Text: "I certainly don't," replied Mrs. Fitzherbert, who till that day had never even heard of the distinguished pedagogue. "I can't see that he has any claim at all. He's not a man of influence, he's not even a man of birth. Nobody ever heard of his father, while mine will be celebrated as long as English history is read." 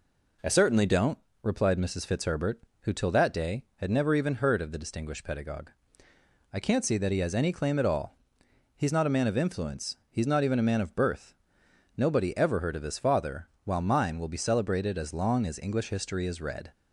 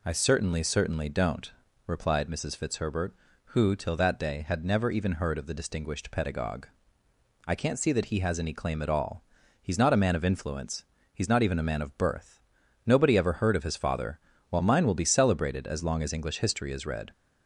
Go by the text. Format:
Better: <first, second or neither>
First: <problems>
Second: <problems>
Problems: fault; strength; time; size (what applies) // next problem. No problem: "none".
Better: first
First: none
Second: says "certainly" twice; at 0.6 s